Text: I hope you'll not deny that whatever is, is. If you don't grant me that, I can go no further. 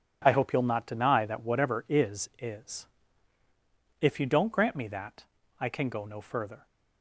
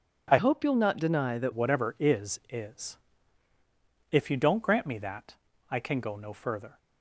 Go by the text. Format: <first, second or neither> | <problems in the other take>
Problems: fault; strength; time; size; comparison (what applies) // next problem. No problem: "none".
first | changes voice from "hope" to "that"; from 0.3 to 1.5 s; 1.2 s long